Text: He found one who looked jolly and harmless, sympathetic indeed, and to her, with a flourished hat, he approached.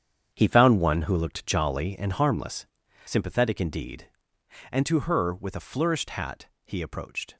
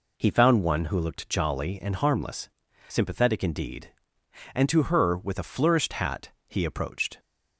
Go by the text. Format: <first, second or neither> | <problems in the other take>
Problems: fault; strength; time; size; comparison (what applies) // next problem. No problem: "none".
second | gets quieter; strong; throughout; 10 dB